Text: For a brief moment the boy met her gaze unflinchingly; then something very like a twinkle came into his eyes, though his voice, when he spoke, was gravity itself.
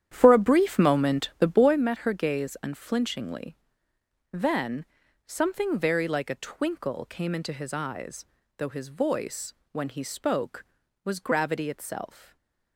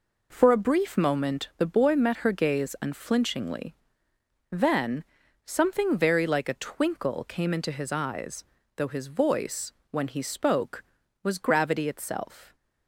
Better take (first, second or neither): second